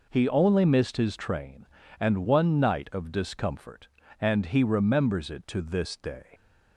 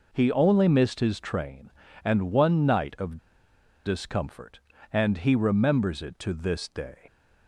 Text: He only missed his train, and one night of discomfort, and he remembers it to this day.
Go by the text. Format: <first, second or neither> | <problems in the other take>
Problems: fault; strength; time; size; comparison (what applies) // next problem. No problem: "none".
first | pauses between "of" and "discomfort"; noticeable; at 3.1 s; 0.67 s long